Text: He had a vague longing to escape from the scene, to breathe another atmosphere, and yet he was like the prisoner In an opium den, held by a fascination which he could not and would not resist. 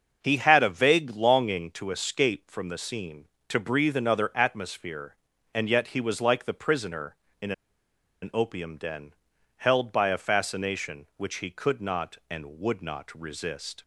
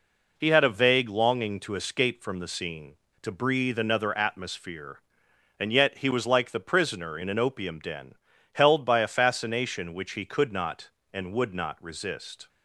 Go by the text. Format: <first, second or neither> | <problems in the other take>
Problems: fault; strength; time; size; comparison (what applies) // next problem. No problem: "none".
second | starts louder than the rest; until 1.2 s; 6.5 dB // pauses between "In" and "an"; noticeable; at 7.5 s; 0.69 s long